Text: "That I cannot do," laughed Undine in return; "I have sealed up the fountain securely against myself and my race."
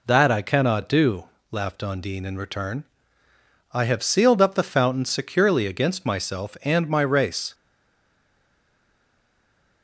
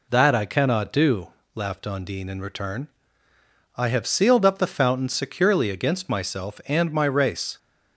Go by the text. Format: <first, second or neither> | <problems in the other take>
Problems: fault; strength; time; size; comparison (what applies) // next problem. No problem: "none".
second | stays silent after the last word; from 7.5 s on; 2.3 s long